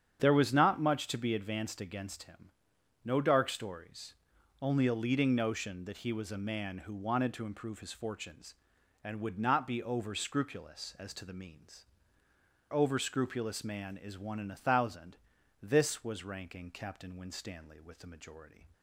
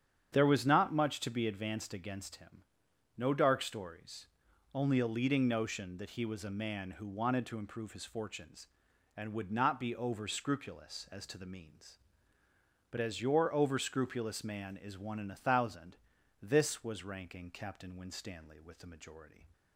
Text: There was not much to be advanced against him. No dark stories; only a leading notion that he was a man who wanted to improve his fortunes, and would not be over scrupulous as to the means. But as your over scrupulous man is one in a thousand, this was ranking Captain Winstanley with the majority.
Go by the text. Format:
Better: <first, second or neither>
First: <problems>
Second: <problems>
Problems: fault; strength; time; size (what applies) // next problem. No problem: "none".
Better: second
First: starts louder than the rest; strong; until 1.2 s; 8 dB // skips "But as your"; at 12.2 s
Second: starts louder than the rest; strong; until 1.3 s; 8 dB